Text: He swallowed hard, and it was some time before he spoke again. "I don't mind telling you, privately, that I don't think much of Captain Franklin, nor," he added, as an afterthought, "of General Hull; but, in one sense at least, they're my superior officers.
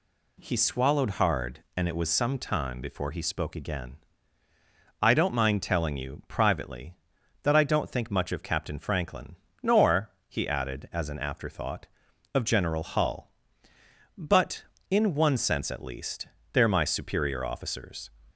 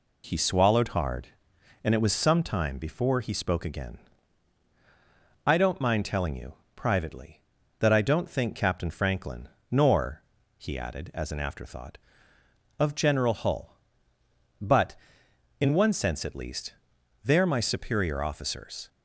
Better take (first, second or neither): first